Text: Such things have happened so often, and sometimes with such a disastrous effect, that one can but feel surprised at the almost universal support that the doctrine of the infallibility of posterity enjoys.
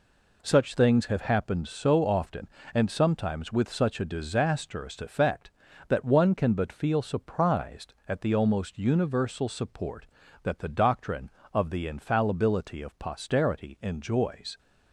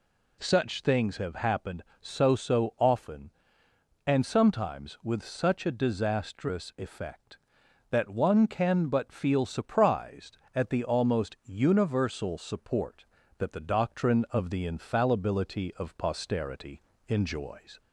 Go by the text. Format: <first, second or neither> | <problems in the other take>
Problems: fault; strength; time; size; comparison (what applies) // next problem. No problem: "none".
first | says "so" twice; at 2.3 s // pauses between "posterity" and "enjoys"; slight; at 16.8 s; 0.26 s long